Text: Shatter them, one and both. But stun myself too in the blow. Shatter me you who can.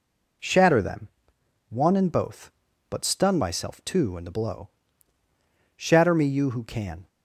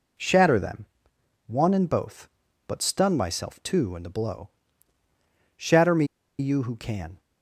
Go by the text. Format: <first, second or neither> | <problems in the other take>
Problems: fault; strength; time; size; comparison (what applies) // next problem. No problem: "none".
first | pauses between "me" and "you"; slight; at 6.0 s; 0.34 s long